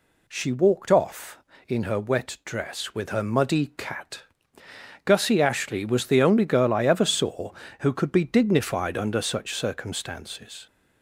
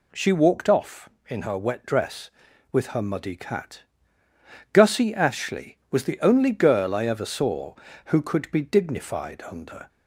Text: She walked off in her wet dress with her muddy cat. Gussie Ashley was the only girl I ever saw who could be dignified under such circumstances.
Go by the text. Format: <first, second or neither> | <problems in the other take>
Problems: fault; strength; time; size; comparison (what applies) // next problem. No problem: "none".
first | stops before "such circumstances"; at 9.8 s